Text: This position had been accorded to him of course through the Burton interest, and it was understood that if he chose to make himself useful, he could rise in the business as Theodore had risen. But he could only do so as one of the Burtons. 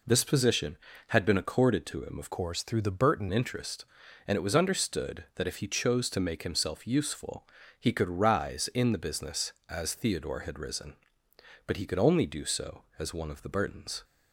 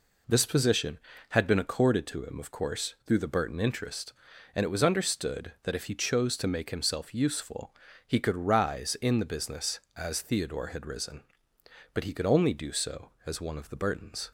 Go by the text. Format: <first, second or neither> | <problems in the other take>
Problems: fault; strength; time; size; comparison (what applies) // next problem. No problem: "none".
second | changes voice from "course" to "Burton"; from 2.3 to 3.2 s; 0.9 s long